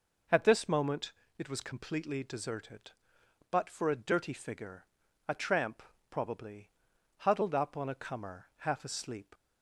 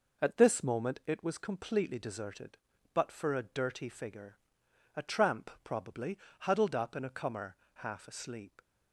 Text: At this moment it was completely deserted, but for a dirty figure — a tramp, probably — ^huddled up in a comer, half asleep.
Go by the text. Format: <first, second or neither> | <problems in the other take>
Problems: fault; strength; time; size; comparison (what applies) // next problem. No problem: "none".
second | pauses between "moment" and "it"; slight; at 1.1 s; 0.26 s long // says "on" for "in"; at 7.7 s